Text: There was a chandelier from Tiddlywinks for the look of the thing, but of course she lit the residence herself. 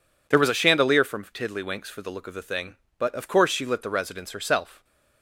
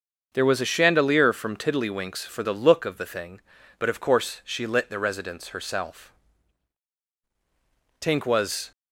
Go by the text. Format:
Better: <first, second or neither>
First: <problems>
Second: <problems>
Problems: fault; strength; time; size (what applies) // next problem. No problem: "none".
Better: first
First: none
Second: starts louder than the rest; until 1.3 s; 6.5 dB // goes on to say "Tink was"; noticeable; from 8.0 s on; 0.70 s long